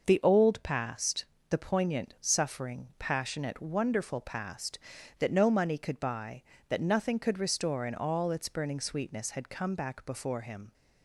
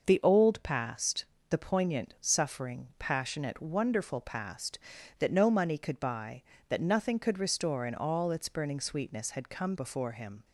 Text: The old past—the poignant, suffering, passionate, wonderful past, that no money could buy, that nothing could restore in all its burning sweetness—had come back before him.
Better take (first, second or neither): first